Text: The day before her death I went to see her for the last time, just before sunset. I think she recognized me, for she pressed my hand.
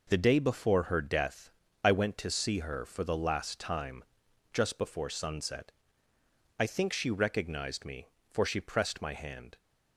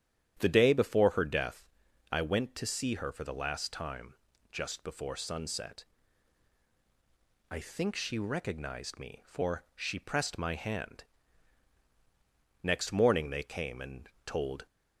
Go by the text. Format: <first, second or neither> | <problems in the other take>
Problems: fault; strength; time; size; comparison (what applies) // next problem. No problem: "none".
first | starts louder than the rest; strong; until 1.4 s; 10 dB // pauses between "death" and "I"; noticeable; at 1.6 s; 0.46 s long; slight in the first // goes on to say "Next morning they came and told"; strong; from 12.6 s on; 2.0 s long